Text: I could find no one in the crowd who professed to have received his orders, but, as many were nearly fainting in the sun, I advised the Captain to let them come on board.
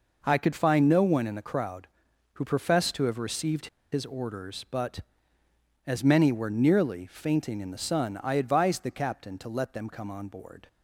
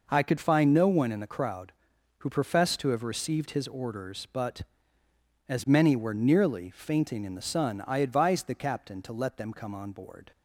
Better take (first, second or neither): second